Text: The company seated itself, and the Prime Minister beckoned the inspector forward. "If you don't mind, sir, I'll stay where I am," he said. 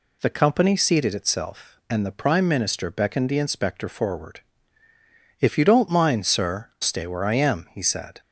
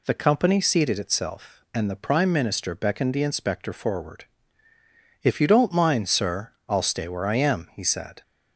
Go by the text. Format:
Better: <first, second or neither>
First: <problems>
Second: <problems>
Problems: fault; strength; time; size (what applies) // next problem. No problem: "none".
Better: second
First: skips "I'll"; at 6.7 s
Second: none